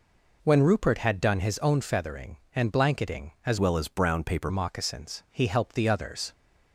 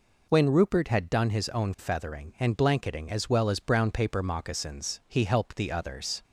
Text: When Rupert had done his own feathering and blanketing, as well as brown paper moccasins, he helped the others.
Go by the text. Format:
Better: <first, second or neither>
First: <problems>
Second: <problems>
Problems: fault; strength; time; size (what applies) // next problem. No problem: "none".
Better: second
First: changes voice from "well" to "paper"; from 3.5 to 4.4 s; 0.9 s long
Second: none